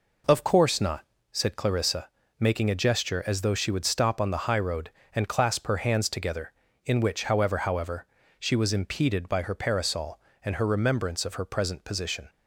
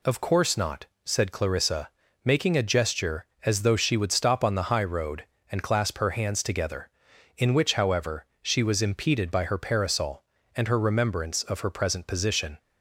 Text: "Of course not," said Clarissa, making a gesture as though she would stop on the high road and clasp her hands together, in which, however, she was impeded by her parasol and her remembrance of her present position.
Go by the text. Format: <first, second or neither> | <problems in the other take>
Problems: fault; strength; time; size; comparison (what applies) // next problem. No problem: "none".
second | says "however" twice; at 7.5 s